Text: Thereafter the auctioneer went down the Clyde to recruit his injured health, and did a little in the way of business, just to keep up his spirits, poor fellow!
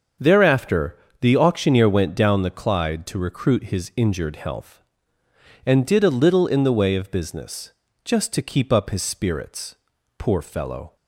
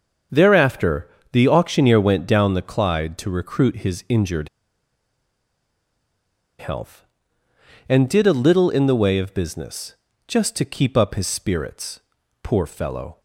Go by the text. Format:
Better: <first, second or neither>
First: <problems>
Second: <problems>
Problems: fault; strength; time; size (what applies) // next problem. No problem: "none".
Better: first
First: starts louder than the rest; until 1.4 s; 6.5 dB // pauses between "Thereafter" and "the"; slight; at 0.9 s; 0.22 s long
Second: starts louder than the rest; until 1.5 s; 6.5 dB // pauses between "Thereafter" and "the"; slight; at 1.0 s; 0.22 s long // pauses between "injured" and "health"; strong; at 4.4 s; 2.1 s long